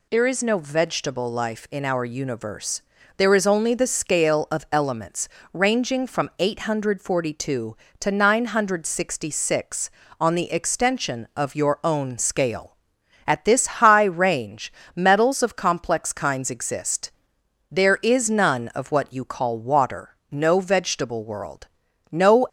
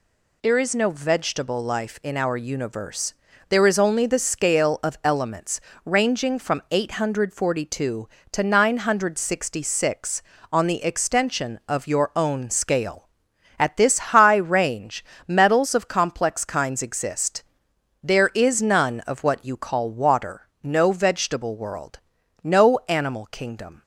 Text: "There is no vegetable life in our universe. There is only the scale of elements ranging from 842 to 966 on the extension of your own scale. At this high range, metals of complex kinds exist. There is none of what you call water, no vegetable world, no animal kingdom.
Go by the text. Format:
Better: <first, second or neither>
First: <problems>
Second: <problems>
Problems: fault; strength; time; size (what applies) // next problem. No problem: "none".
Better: second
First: pauses between "elements" and "ranging"; slight; at 5.2 s; 0.24 s long // pauses between "this" and "high"; slight; at 13.6 s; 0.16 s long // stops before "animal kingdom"; at 22.4 s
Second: pauses between "elements" and "ranging"; slight; at 5.5 s; 0.24 s long // pauses between "this" and "high"; slight; at 13.9 s; 0.16 s long